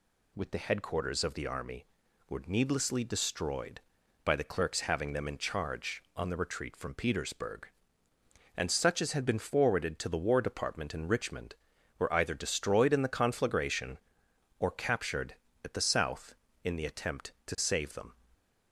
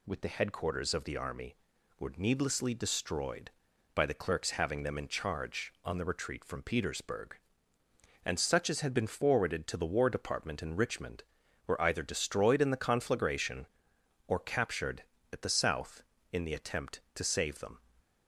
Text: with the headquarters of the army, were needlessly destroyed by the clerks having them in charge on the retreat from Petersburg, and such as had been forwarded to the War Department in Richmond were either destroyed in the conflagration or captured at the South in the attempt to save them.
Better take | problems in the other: neither | none

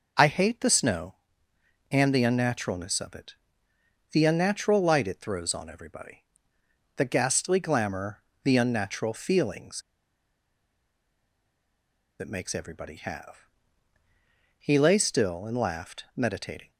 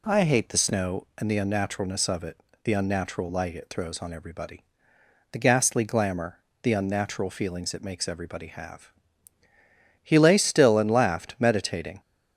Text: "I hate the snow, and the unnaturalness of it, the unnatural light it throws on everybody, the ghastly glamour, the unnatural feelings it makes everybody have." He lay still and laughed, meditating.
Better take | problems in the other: second | pauses between "feelings" and "it"; strong; at 9.8 s; 2.3 s long

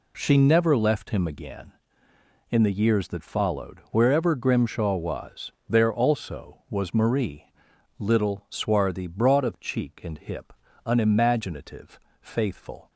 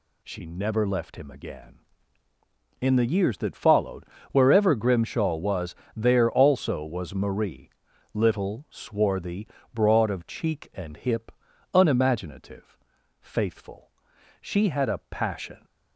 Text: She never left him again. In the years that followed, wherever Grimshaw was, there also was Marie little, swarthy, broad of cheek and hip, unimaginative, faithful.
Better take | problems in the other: first | pauses between "Marie" and "little"; noticeable; at 7.6 s; 0.46 s long; noticeable in the first // goes on to say "She had a passion"; noticeable; from 14.4 s on; 1.2 s long

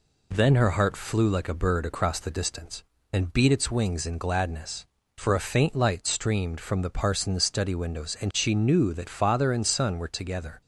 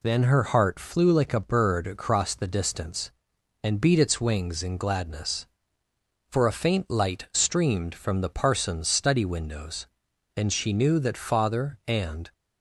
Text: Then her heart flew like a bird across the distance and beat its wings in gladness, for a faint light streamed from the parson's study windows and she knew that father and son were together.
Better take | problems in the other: first | stops before "son were together"; at 12.3 s

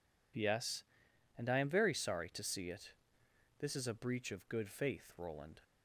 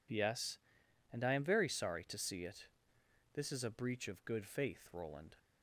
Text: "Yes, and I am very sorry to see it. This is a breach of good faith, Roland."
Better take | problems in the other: neither | none

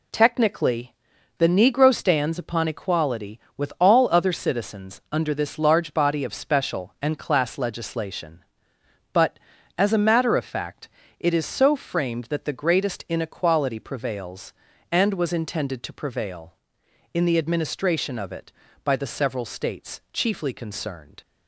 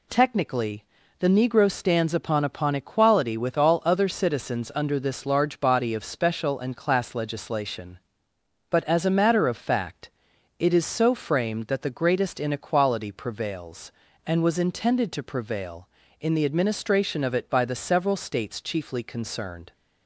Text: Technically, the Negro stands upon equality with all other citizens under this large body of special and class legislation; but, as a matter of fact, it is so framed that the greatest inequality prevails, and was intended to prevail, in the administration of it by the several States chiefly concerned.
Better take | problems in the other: first | says "upon" twice; at 2.4 s

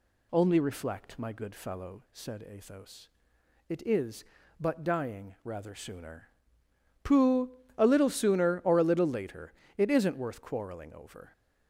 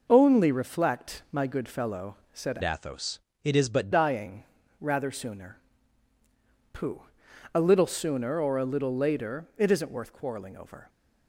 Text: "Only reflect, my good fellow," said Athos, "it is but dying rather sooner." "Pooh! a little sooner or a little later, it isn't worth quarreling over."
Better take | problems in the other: first | changes voice from "Athos" to "but"; from 2.6 to 3.9 s; 1.3 s long // pauses between "dying" and "rather"; slight; at 4.4 s; 0.36 s long

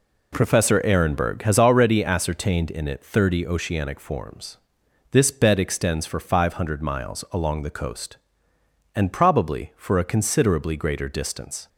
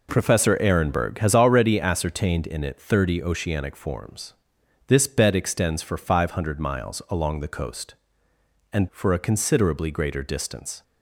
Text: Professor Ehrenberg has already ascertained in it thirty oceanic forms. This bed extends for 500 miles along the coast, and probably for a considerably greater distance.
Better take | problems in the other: first | skips "probably"; at 8.8 s

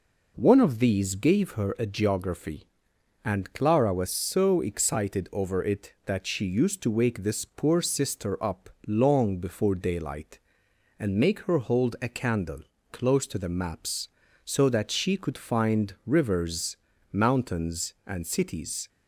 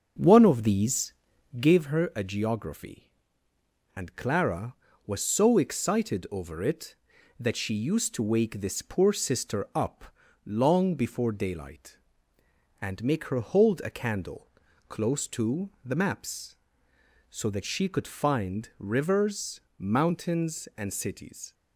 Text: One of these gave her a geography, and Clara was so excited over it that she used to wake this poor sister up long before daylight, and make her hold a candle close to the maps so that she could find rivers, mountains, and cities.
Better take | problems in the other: first | starts louder than the rest; noticeable; until 1.8 s; 6 dB // pauses between "these" and "gave"; noticeable; at 1.1 s; 0.46 s long // pauses between "up" and "long"; at 10.0 s; 0.38 s long; slight in the first // pauses between "candle" and "close"; at 14.4 s; 0.42 s long; slight in the first // pauses between "to" and "the"; slight; at 15.6 s; 0.16 s long

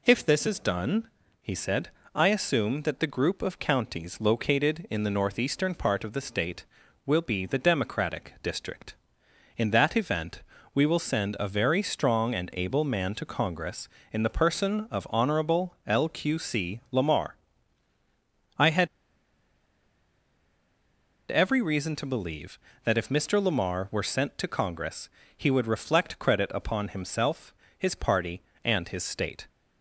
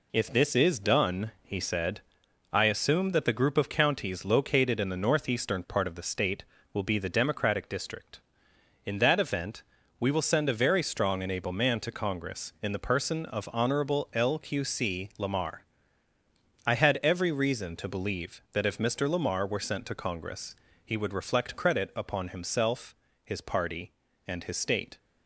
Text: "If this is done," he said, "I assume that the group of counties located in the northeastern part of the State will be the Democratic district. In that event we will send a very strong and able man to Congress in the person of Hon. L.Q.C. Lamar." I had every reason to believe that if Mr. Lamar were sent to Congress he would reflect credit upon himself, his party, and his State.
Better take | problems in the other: second | pauses between "event" and "we"; slight; at 10.4 s; 0.32 s long; slight in the second // pauses between "had" and "every"; strong; at 18.8 s; 2.4 s long // pauses between "Congress" and "he"; slight; at 25.0 s; 0.28 s long; slight in the second

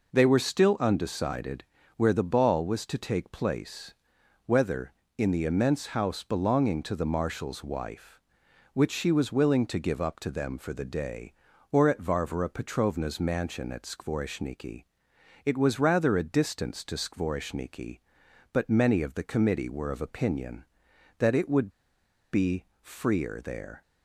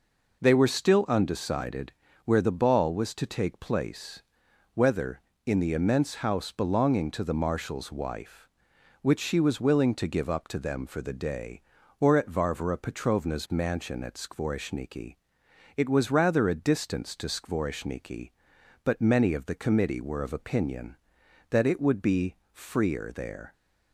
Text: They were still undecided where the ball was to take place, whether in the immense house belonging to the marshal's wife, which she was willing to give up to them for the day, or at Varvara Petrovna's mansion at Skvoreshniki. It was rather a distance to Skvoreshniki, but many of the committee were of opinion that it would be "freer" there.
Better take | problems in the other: second | pauses between "undecided" and "where"; slight; at 1.6 s; 0.32 s long; slight in the second // pauses between "would" and "be"; noticeable; at 21.6 s; 0.63 s long // pauses between "be" and "freer"; slight; at 22.6 s; 0.16 s long; slight in the second

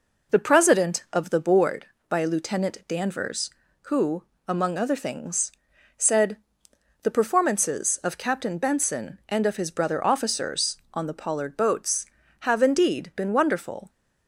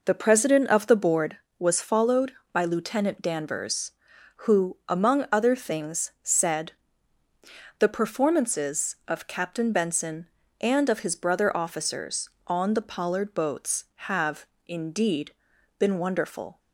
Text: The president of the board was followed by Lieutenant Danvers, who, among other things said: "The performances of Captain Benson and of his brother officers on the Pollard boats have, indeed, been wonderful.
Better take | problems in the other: second | skips "was followed"; at 1.9 s // pauses between "things" and "said"; noticeable; at 5.5 s; 0.46 s long

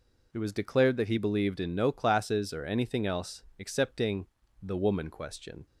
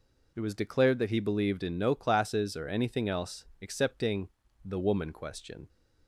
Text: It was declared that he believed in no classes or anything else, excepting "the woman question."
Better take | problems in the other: neither | pauses between "excepting" and "the"; slight; the same in both

